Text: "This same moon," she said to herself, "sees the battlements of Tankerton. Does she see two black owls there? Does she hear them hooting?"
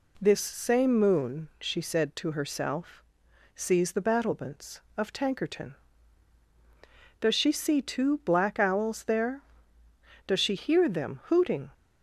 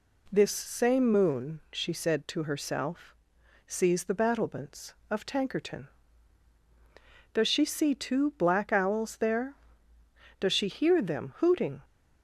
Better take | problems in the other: neither | none

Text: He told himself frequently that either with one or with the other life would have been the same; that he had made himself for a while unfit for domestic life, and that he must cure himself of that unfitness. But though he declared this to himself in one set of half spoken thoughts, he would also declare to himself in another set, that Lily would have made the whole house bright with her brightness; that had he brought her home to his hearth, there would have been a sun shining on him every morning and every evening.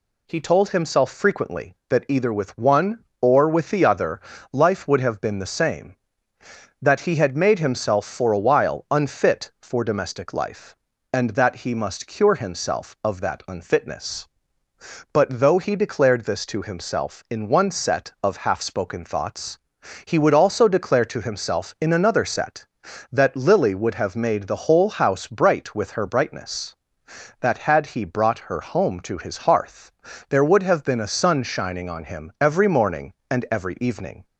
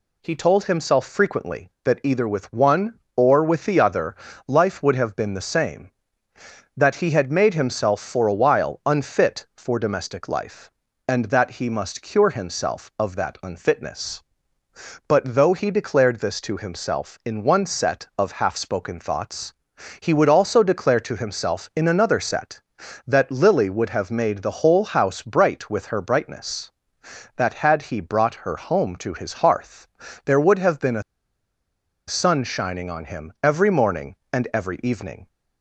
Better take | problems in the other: first | pauses between "other" and "life"; slight; at 4.1 s; 0.32 s long; slight in the first // pauses between "a" and "sun"; at 31.0 s; 1.0 s long

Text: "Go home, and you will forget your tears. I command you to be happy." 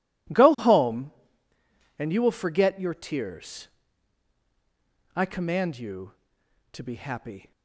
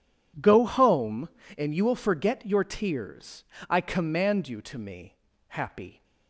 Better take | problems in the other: first | says "me" for "be"; at 4.7 s

